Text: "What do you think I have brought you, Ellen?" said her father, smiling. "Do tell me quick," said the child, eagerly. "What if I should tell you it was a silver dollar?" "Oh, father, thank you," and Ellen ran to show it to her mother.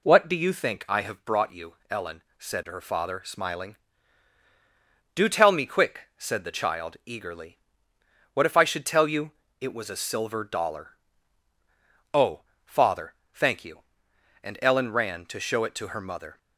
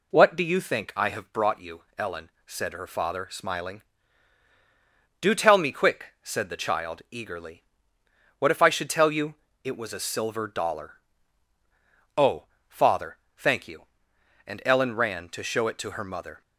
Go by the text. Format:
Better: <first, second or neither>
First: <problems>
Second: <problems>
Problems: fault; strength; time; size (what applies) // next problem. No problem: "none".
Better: neither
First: pauses between "you" and "it"; slight; at 9.3 s; 0.28 s long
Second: pauses between "you" and "it"; slight; at 9.3 s; 0.28 s long